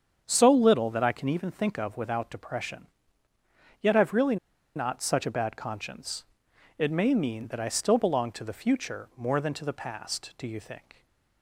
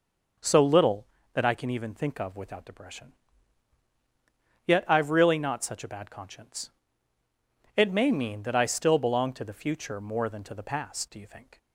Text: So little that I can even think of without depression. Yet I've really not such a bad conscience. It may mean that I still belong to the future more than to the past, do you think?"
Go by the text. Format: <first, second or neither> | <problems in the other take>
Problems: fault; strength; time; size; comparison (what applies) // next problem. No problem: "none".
second | starts louder than the rest; strong; until 1.2 s; 7.5 dB // pauses between "really" and "not"; at 4.3 s; 0.39 s long